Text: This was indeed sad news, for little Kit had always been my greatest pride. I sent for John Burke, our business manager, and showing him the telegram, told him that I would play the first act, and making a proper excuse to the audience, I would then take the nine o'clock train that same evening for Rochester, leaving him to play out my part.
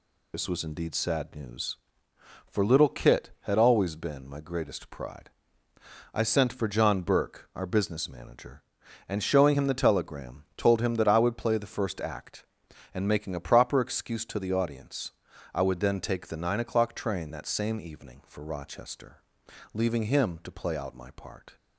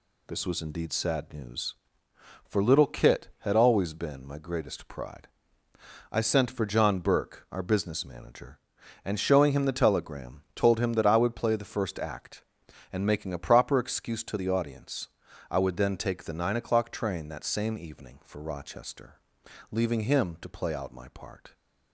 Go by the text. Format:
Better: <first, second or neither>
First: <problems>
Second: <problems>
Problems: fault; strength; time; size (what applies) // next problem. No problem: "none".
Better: second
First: loses the start of "This"; at 0.3 s; 40 ms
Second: none